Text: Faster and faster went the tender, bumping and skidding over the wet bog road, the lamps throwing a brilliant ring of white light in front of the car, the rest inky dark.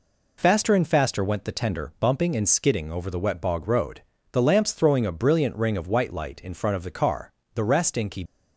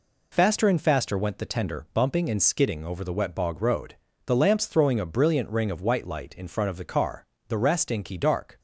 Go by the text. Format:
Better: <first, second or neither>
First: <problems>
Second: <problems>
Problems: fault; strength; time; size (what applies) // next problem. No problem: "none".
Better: second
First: stops before "dark"; at 8.2 s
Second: none